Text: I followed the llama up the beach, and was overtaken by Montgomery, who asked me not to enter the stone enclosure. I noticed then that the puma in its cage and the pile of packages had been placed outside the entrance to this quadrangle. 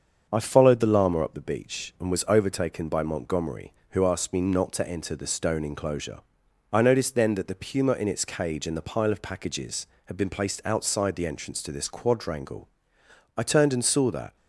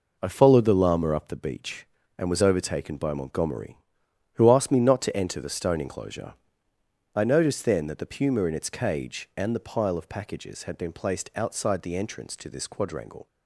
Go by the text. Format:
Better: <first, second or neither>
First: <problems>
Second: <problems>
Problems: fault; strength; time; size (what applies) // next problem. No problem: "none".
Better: second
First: starts louder than the rest; until 1.3 s; 7 dB // goes on to say "I turned and saw that"; noticeable; from 13.3 s on; 0.98 s long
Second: none